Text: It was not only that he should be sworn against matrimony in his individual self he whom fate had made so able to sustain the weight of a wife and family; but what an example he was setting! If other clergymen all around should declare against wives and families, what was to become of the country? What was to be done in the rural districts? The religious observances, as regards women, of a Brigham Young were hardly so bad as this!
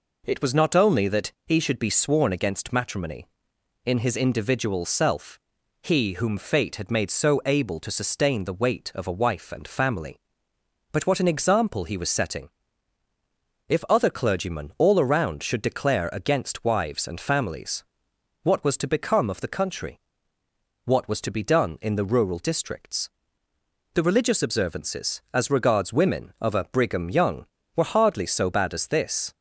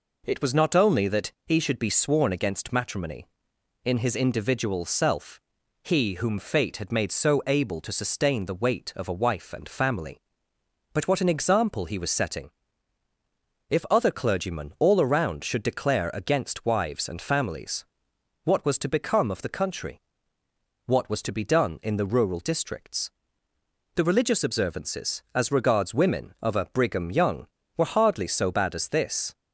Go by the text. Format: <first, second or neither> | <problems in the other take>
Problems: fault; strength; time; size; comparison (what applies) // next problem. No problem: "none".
neither | pauses between "self" and "he"; the same in both